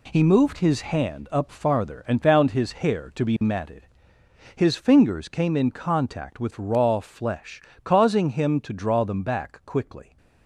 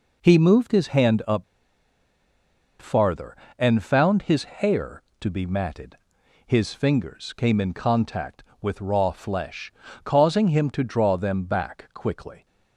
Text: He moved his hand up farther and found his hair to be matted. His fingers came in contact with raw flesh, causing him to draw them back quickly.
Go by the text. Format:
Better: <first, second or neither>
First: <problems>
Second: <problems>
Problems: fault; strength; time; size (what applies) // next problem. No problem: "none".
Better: first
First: none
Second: pauses between "up" and "farther"; strong; at 1.4 s; 1.3 s long